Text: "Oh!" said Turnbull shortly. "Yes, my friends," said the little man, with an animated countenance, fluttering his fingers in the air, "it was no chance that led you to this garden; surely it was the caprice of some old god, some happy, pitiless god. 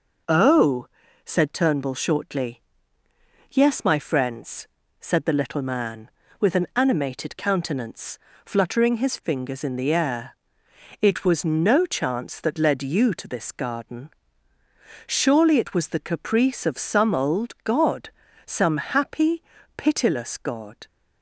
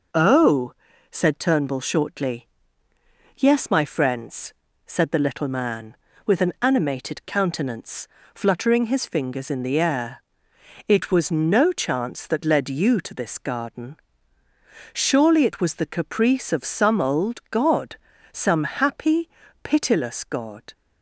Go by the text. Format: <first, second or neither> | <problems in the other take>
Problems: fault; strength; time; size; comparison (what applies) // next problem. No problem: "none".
neither | none